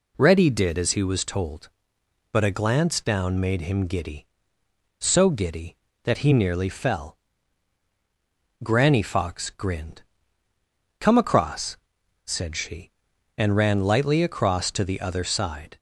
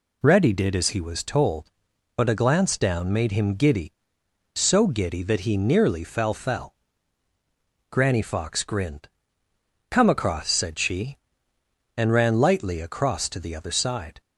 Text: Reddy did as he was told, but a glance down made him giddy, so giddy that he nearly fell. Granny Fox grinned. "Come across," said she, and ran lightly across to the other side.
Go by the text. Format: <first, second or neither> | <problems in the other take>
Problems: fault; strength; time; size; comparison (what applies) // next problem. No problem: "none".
first | says "fell" twice; at 6.3 s